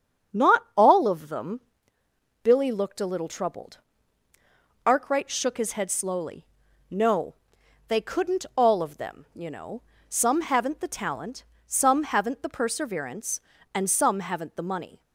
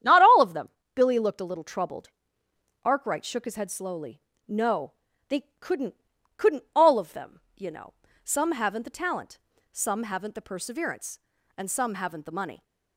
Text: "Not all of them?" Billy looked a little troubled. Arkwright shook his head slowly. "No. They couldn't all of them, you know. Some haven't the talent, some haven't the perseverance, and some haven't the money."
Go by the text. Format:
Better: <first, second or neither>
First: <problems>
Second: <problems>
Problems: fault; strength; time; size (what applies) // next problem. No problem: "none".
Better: first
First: starts louder than the rest; strong; until 1.4 s; 7.5 dB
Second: starts louder than the rest; strong; until 1.2 s; 10 dB // says "couldn't" twice; at 6.3 s